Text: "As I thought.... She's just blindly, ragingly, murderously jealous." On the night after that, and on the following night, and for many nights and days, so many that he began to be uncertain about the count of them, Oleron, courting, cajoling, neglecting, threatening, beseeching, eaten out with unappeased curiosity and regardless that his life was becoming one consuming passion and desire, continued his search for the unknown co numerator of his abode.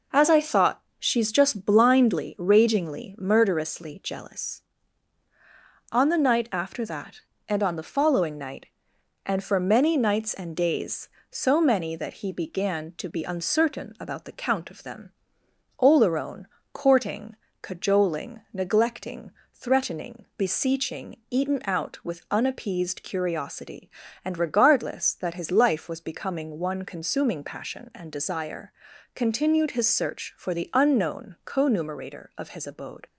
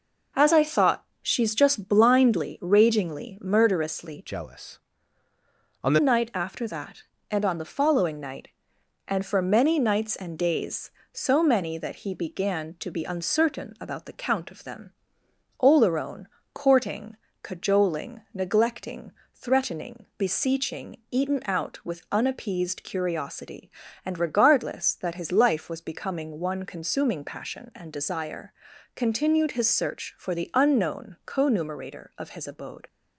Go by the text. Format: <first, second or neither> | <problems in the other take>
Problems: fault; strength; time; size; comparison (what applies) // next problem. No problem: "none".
first | changes voice from "jealous" to "the"; from 4.2 to 5.9 s; 1.7 s long